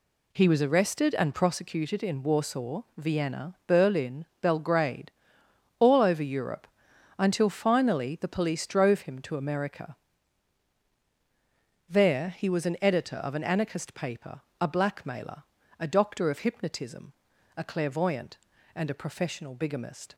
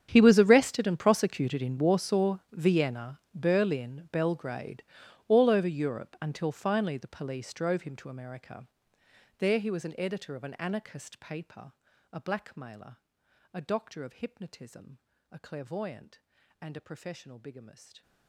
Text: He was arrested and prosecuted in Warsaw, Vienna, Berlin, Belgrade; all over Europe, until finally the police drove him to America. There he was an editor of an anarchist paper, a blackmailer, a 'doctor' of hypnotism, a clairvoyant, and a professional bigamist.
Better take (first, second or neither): first